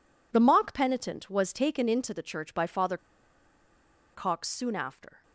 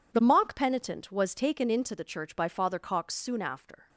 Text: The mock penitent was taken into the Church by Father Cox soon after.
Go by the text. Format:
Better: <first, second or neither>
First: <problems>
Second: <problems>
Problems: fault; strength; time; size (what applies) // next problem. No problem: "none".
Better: second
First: pauses between "Father" and "Cox"; at 2.9 s; 1.1 s long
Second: none